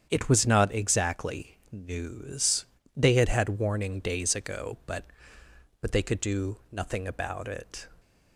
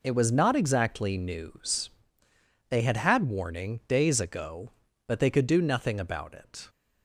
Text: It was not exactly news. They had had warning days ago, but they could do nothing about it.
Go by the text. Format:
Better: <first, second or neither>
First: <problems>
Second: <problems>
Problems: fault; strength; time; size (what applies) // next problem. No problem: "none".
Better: second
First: starts louder than the rest; strong; until 1.1 s; 8 dB // says "but" twice; at 5.8 s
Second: none